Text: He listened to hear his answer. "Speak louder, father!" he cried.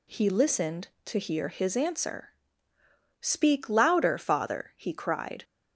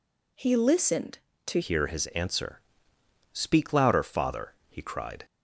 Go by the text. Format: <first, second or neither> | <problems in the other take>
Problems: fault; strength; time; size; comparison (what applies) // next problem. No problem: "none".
first | changes voice at "hear"; from 1.6 s on; 3.6 s long